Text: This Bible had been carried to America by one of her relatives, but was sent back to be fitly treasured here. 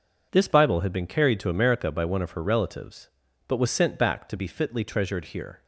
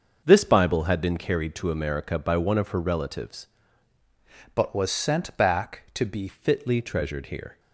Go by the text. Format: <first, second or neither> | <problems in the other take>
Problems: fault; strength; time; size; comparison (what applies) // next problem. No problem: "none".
first | starts louder than the rest; until 1.2 s; 6 dB // changes voice from "but" to "be"; from 4.5 to 6.2 s; 1.7 s long